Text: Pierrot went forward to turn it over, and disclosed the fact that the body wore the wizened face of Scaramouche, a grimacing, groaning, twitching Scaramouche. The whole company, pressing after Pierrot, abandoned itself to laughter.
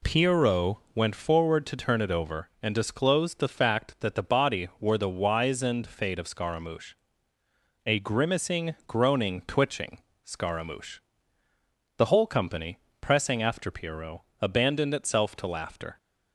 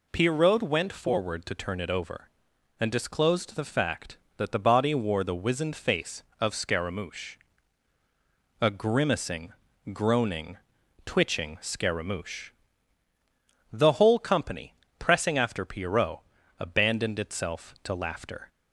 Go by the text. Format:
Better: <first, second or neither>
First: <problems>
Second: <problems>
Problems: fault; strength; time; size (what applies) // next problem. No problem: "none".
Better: second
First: pauses between "Pierrot" and "went"; slight; at 0.7 s; 0.16 s long // says "fate" for "face"; at 5.8 s // pauses between "twitching" and "Scaramouche"; slight; at 9.9 s; 0.24 s long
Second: none